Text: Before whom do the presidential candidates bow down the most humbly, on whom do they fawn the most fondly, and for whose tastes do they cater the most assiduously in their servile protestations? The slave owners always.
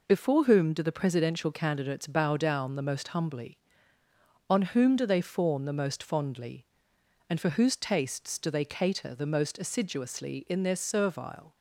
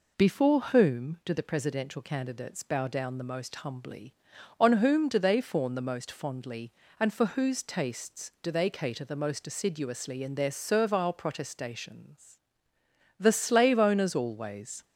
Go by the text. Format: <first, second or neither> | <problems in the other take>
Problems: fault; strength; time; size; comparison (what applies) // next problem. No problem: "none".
second | stops before "protestations The slave owners always"; at 11.5 s